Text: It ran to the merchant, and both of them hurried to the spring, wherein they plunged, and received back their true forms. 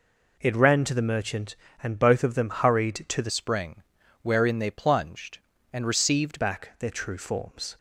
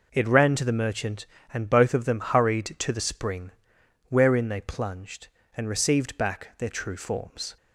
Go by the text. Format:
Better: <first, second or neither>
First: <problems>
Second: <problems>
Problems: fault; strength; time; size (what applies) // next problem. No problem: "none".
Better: second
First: changes voice from "spring" to "received"; from 3.3 to 6.4 s; 3.1 s long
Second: none